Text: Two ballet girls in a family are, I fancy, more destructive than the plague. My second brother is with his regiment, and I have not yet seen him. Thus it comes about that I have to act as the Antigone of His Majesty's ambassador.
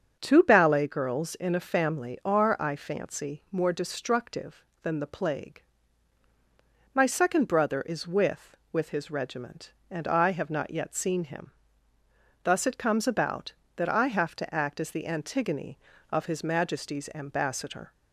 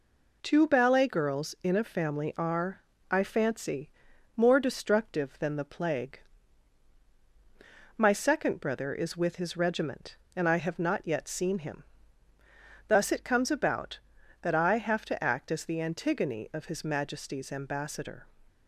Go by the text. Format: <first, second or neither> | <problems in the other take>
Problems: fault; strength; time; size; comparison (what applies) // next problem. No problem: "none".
second | starts louder than the rest; strong; until 1.2 s; 7 dB // says "with" twice; at 8.7 s